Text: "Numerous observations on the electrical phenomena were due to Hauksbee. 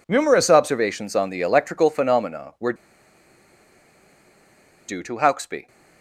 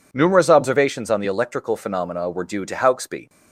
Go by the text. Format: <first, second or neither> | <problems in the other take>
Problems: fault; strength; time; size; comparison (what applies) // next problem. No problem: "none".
second | pauses between "were" and "due"; strong; at 2.7 s; 2.1 s long